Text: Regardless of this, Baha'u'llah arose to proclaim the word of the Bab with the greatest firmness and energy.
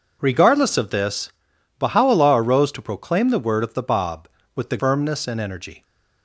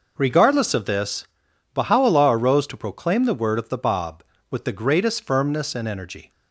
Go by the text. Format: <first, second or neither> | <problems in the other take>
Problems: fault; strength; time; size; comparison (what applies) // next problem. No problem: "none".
second | skips "greatest"; at 4.7 s